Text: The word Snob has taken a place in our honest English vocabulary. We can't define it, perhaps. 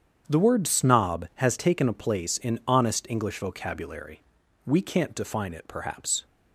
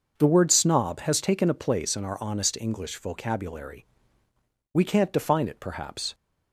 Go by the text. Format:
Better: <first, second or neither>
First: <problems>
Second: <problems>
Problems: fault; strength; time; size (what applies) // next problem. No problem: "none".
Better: second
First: starts louder than the rest; strong; until 1.2 s; 8.5 dB // skips "our"; at 2.6 s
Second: starts louder than the rest; noticeable; until 1.1 s; 6 dB